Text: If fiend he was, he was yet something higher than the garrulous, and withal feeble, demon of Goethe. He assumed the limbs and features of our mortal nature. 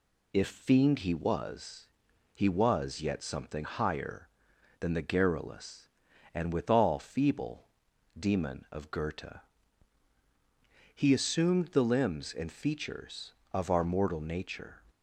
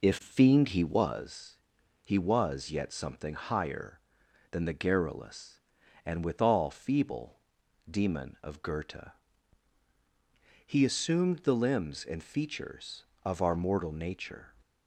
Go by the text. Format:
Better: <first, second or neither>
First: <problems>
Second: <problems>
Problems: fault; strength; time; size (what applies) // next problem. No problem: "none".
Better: first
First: none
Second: starts louder than the rest; noticeable; until 1.3 s; 4 dB